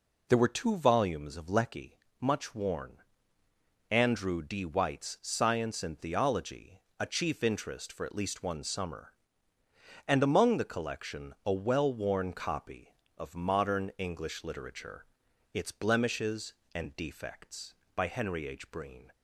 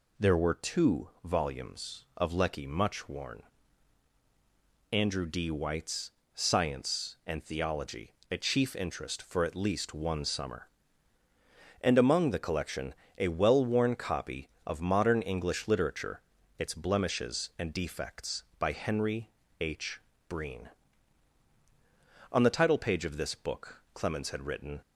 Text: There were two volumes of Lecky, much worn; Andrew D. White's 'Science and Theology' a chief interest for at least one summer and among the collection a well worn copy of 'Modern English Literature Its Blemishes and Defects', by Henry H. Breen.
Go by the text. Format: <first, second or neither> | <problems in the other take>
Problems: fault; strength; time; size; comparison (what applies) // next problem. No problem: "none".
first | pauses between "White's" and "Science"; slight; at 6.0 s; 0.24 s long // pauses between "Theology" and "a"; slight; at 8.1 s; 0.18 s long; slight in the first // pauses between "collection" and "a"; slight; at 12.9 s; 0.22 s long // pauses between "Literature" and "Its"; at 16.2 s; 0.38 s long; noticeable in the first // pauses between "Henry" and "H"; slight; at 19.3 s; 0.28 s long // goes on to say "On the title page of this book Clemens had written"; strong; from 22.3 s on; 2.5 s long